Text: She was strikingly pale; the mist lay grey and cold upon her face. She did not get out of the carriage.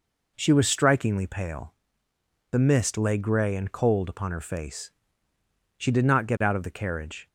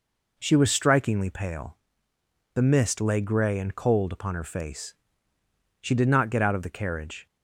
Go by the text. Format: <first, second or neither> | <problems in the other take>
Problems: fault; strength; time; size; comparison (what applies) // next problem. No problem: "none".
neither | none